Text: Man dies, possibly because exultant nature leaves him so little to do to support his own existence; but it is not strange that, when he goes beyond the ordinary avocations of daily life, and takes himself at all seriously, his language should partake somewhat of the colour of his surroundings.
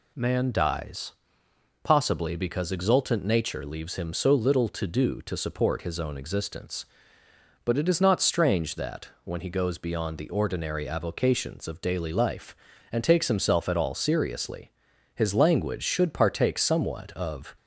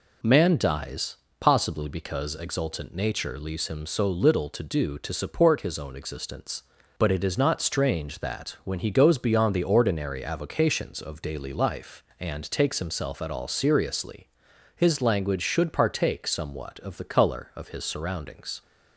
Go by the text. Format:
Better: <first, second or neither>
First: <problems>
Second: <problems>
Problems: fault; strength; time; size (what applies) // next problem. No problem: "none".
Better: second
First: stops before "the colour of his surroundings"; at 17.5 s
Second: none